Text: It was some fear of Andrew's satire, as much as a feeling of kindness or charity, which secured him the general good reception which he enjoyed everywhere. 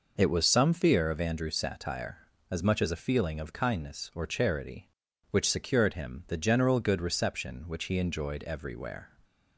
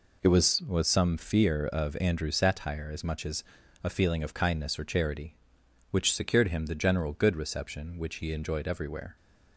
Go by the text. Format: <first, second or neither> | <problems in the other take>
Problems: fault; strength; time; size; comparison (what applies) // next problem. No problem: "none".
first | says "was" twice; at 0.6 s // pauses between "as" and "a"; at 3.4 s; 0.42 s long